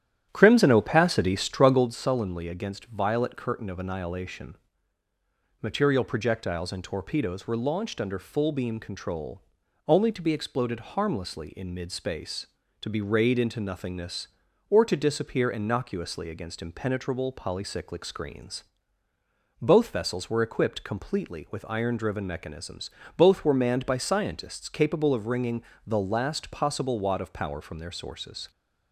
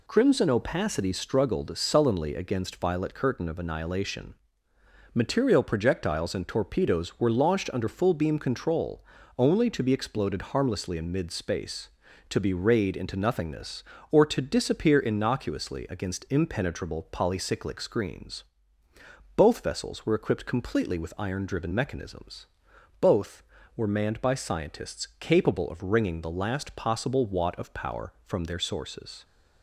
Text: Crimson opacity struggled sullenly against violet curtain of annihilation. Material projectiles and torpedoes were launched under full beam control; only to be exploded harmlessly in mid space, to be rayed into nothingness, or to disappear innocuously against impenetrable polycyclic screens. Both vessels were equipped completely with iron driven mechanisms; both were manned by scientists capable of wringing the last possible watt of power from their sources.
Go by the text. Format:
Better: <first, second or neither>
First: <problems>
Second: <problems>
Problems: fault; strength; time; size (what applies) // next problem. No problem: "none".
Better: second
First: starts louder than the rest; strong; until 1.9 s; 11 dB // pauses between "wringing" and "the"; slight; at 25.6 s; 0.22 s long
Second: none